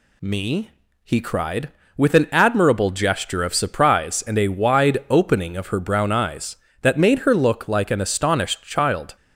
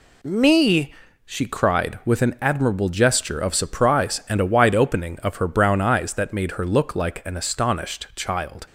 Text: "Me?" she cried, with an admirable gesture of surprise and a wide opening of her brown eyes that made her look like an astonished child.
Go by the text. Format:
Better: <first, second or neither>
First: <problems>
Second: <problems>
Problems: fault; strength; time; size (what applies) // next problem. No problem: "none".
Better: second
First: says "he" for "she"; at 1.0 s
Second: none